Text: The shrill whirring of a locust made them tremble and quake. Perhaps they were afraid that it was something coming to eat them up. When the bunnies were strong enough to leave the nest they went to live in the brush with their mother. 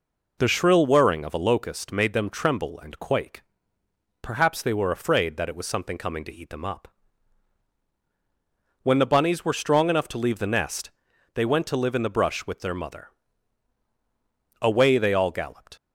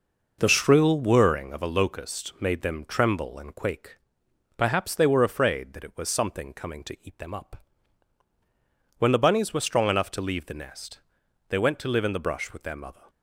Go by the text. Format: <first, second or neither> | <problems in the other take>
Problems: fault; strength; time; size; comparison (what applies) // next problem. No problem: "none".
second | pauses between "nest" and "they"; at 10.8 s; 0.44 s long; noticeable in the second // goes on to say "Away they all galloped"; noticeable; from 14.5 s on; 1.1 s long